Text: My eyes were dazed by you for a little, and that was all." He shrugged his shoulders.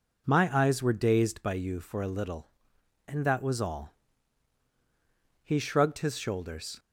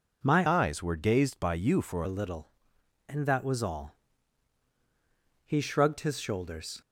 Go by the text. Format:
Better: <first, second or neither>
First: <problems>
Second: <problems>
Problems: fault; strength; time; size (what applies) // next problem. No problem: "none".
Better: first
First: none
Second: changes voice from "eyes" to "for"; from 0.4 to 2.0 s; 1.6 s long